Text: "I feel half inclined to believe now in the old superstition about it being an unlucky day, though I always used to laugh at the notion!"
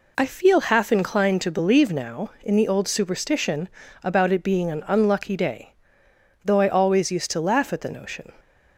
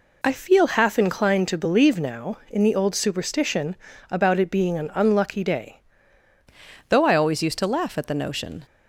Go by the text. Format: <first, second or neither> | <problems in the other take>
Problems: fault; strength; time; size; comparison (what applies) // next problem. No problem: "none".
first | pauses between "superstition" and "about"; slight; at 3.7 s; 0.36 s long; slight in the first // changes voice at "though"; from 6.8 s on; 1.8 s long